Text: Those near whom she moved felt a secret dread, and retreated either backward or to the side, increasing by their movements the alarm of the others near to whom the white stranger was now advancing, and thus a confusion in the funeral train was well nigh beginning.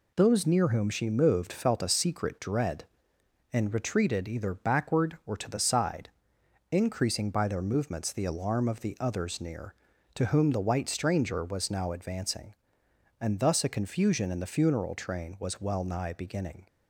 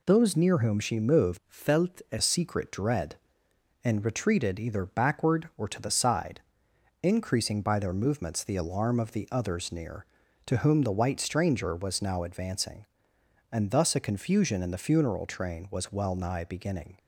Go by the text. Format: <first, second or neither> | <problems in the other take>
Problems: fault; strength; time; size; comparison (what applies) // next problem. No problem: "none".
first | changes voice from "felt" to "a"; from 1.4 to 2.1 s; 0.7 s long